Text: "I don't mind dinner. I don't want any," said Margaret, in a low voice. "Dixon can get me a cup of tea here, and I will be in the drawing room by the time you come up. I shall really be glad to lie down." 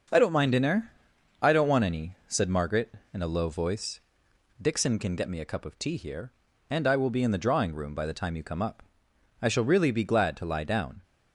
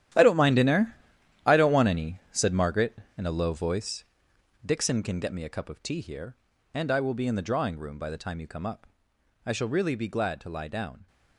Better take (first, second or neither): first